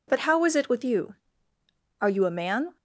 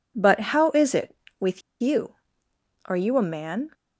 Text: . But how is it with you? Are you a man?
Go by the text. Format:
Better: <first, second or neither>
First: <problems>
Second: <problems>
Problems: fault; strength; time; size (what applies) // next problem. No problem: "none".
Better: first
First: none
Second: pauses between "with" and "you"; slight; at 1.6 s; 0.19 s long